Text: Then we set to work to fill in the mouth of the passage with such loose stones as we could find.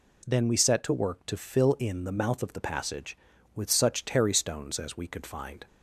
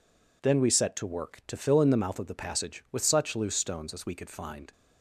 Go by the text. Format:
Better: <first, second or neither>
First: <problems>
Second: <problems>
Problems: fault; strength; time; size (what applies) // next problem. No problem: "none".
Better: second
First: says "terry" for "loose"; at 4.0 s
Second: none